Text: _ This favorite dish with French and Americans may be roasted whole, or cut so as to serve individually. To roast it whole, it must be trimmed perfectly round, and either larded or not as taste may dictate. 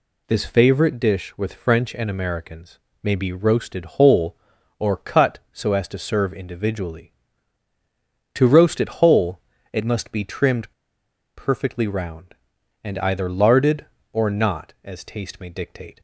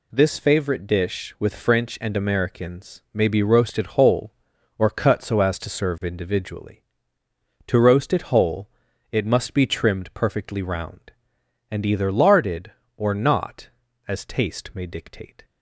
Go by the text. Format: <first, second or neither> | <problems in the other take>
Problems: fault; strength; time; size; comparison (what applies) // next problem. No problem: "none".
second | pauses between "Americans" and "may"; slight; at 2.7 s; 0.24 s long // pauses between "trimmed" and "perfectly"; noticeable; at 10.7 s; 0.64 s long